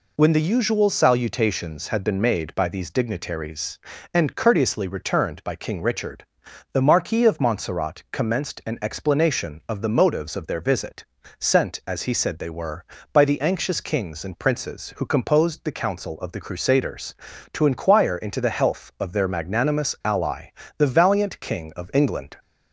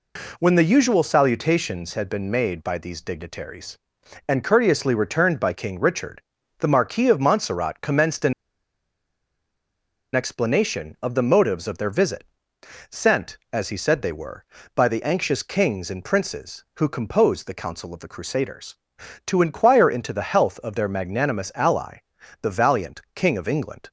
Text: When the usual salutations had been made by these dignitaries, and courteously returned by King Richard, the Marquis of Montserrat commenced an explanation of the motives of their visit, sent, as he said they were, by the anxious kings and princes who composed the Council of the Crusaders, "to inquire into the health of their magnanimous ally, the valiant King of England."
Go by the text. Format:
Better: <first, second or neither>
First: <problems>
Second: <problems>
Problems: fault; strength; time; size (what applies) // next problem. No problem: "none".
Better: first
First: none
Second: pauses between "an" and "explanation"; strong; at 8.3 s; 1.8 s long